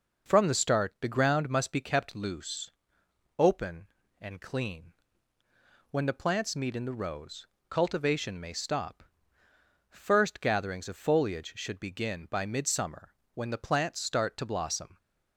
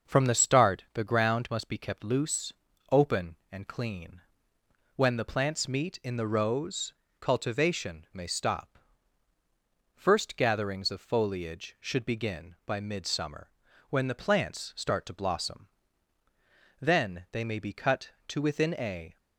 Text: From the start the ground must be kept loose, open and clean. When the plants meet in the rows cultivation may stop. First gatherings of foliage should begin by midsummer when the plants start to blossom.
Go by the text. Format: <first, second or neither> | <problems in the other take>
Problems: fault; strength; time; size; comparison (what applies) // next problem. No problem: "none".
first | starts louder than the rest; until 1.1 s; 6 dB // pauses between "rows" and "cultivation"; slight; at 6.9 s; 0.26 s long; slight in the first // pauses between "midsummer" and "when"; at 13.4 s; 0.42 s long; slight in the first // goes on to say "Then they may be cut to within a"; strong; from 16.7 s on; 2.3 s long